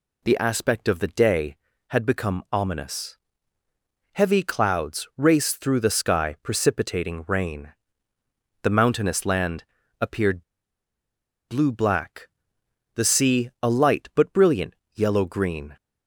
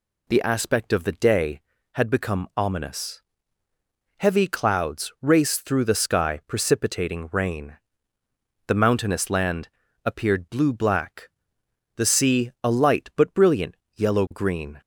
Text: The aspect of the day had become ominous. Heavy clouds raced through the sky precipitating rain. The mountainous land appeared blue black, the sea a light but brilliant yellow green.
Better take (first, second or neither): second